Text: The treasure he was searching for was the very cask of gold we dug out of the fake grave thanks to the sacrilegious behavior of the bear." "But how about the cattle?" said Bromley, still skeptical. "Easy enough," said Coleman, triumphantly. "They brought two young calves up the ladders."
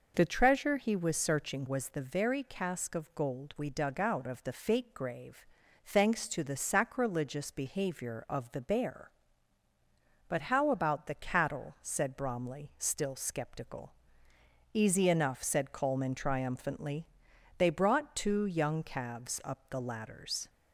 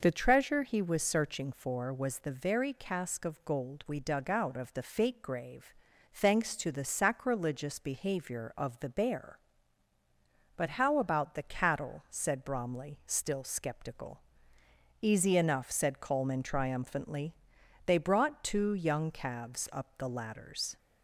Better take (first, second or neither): second